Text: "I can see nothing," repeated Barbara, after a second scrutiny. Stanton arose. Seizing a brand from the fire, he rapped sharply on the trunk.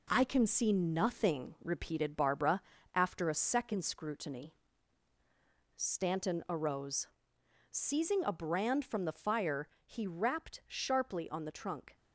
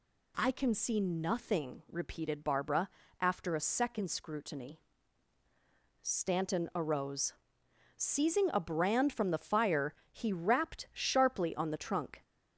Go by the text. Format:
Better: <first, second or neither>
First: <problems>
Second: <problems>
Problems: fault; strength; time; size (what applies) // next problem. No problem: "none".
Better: second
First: gets quieter; noticeable; throughout; 5.5 dB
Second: none